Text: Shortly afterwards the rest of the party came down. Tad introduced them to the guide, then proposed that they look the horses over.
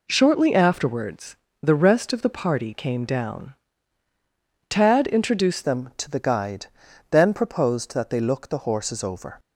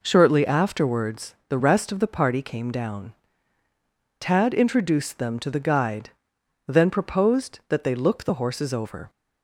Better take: second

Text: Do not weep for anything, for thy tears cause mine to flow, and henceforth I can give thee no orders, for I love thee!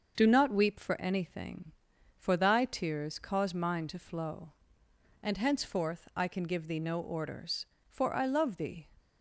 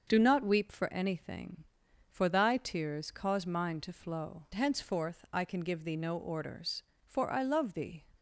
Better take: first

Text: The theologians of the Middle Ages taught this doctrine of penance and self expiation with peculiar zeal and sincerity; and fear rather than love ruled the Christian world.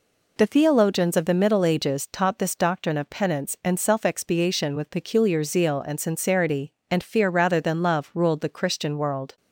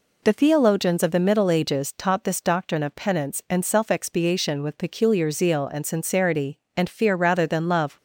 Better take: first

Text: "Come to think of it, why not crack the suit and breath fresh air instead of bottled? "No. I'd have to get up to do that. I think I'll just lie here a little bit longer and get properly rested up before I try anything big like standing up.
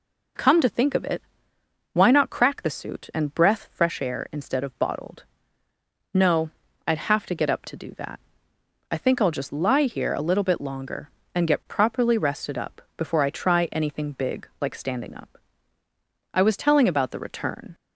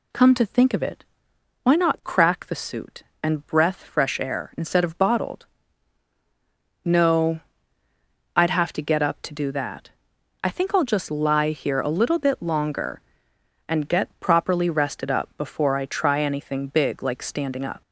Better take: second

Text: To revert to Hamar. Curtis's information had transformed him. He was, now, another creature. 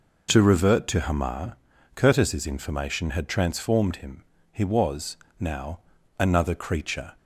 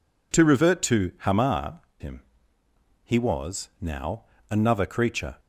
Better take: first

